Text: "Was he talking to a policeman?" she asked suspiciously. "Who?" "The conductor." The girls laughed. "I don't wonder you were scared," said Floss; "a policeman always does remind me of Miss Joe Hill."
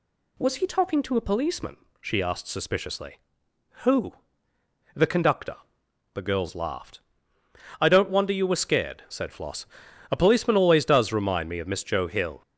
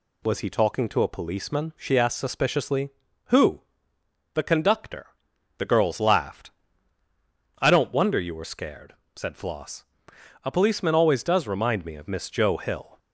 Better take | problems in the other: neither | none

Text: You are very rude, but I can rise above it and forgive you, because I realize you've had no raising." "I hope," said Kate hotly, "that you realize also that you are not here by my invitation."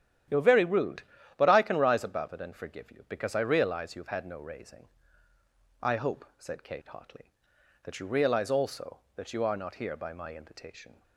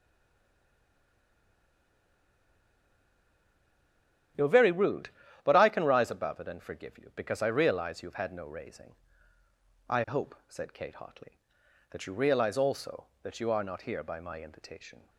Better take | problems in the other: first | stays silent before the first word; strong; until 4.3 s; 4.3 s long // starts louder than the rest; strong; until 5.7 s; 10.5 dB; strong in the first

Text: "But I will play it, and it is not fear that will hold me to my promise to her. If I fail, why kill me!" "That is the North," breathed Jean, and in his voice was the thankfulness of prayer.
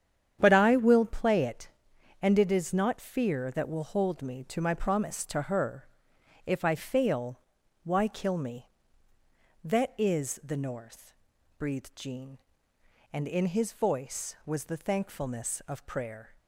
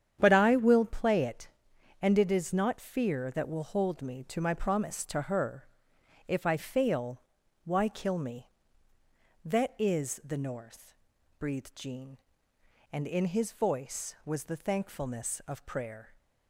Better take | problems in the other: neither | starts louder than the rest; strong; the same in both

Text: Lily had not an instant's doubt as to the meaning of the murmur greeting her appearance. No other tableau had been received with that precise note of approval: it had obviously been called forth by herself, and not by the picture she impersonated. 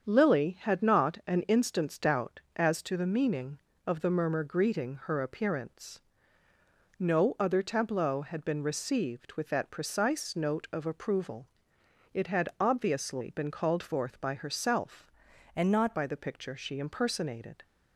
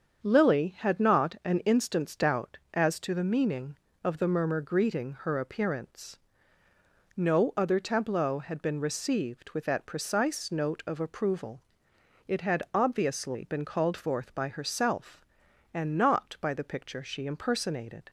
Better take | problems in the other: second | starts louder than the rest; strong; until 1.1 s; 7 dB; strong in the second // changes voice from "and" to "not"; from 15.5 to 15.9 s; 0.4 s long

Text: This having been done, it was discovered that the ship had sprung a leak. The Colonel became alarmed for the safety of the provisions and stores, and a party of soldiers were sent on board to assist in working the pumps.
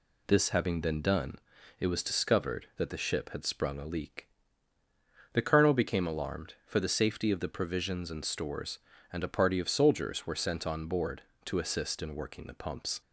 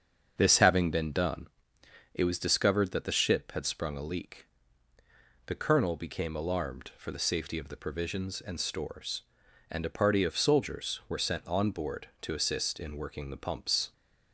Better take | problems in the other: first | starts louder than the rest; until 1.6 s; 7 dB

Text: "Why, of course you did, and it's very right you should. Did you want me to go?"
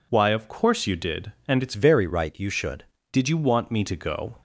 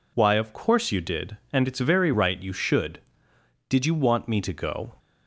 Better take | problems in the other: second | changes voice from "very" to "should"; from 1.7 to 2.8 s; 1.1 s long

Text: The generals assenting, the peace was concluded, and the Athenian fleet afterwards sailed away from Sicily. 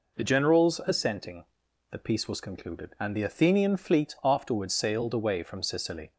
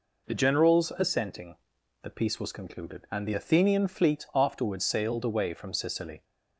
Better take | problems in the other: neither | none

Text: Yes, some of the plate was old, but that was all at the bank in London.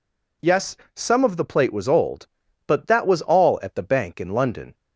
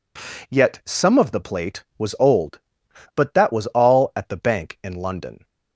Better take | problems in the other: first | says "Yet" for "Yes"; at 0.4 s

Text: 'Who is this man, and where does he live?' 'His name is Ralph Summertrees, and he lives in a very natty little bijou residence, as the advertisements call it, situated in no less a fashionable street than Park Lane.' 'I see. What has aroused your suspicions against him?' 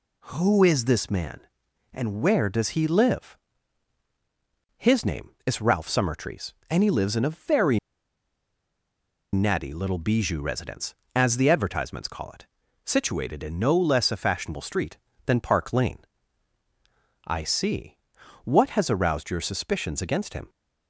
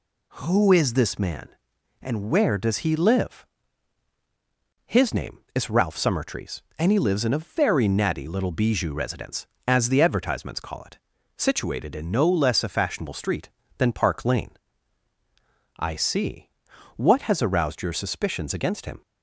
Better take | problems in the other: second | pauses between "very" and "natty"; strong; at 7.7 s; 1.5 s long

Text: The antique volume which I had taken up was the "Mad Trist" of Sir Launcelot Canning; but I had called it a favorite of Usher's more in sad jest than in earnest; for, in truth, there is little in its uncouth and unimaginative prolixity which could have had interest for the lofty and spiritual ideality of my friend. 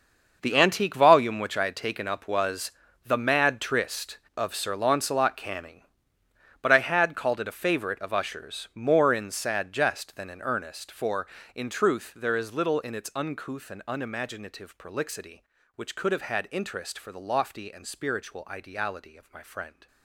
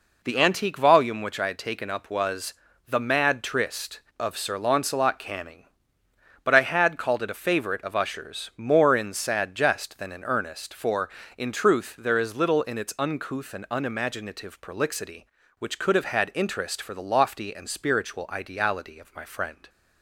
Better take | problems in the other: second | gets quieter; strong; throughout; 14.5 dB // pauses between "was" and "the"; slight; at 2.7 s; 0.34 s long; slight in the second

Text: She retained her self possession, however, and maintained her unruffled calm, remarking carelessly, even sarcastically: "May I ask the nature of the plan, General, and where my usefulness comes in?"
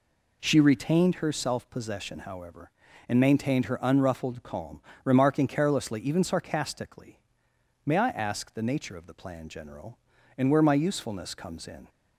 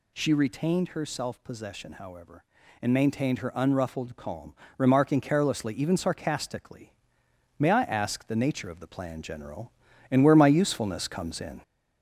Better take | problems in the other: first | gets louder; slight; throughout; 2.5 dB

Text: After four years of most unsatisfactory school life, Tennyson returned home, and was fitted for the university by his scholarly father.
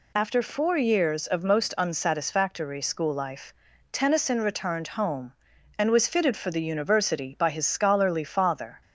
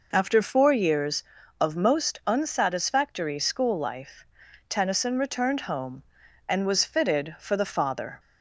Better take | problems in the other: first | skips "university by his scholarly"; at 7.7 s

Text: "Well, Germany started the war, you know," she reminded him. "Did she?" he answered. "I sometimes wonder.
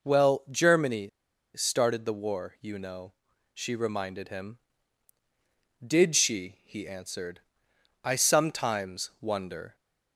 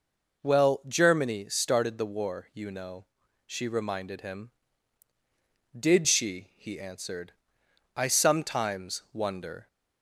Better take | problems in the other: second | pauses between "Germany" and "started"; noticeable; at 1.0 s; 0.47 s long

